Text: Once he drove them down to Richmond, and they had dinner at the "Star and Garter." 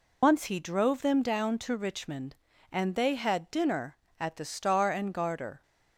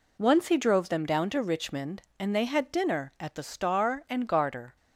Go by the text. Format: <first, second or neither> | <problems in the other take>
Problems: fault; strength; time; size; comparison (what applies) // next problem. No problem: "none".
second | loses the start of "Once"; at 0.2 s; 110 ms